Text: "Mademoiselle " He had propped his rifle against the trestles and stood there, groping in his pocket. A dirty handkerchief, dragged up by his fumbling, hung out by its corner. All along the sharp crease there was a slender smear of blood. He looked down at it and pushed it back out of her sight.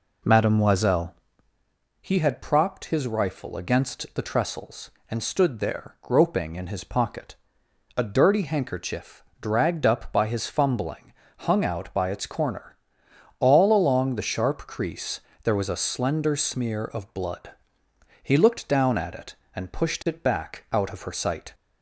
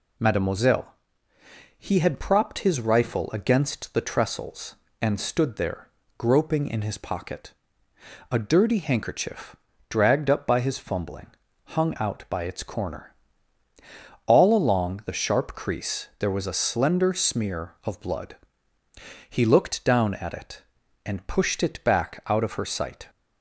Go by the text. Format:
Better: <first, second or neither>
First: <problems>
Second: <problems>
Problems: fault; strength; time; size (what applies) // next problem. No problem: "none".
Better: second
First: starts louder than the rest; noticeable; until 1.7 s; 4 dB // pauses between "crease" and "there"; slight; at 15.2 s; 0.22 s long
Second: none